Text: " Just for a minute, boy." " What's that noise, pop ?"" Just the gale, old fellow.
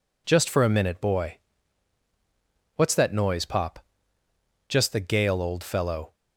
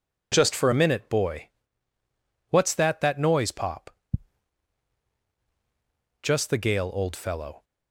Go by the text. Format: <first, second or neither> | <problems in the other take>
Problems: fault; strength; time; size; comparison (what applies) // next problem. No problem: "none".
first | starts louder than the rest; strong; until 1.3 s; 8 dB // says "that" twice; at 3.0 s